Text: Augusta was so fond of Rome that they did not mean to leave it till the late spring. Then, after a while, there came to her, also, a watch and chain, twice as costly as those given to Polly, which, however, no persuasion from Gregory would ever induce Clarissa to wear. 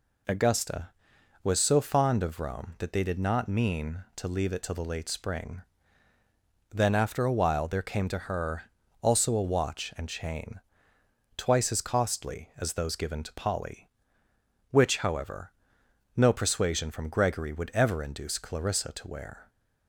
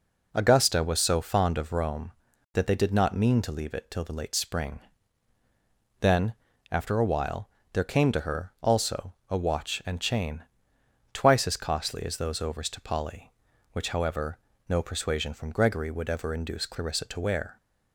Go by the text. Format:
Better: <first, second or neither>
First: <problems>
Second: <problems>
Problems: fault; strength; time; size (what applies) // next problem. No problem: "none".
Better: first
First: none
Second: says "overs" for "given"; at 12.4 s